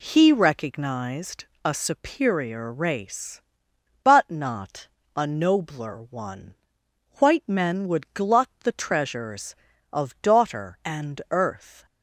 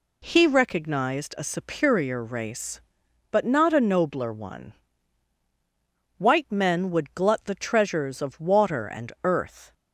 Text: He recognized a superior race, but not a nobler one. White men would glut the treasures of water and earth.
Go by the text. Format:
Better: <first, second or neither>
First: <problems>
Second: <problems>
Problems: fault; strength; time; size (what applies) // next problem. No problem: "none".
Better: second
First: pauses between "recognized" and "a"; slight; at 1.4 s; 0.18 s long // pauses between "not" and "a"; slight; at 4.8 s; 0.28 s long // says "daughter" for "water"; at 10.2 s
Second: none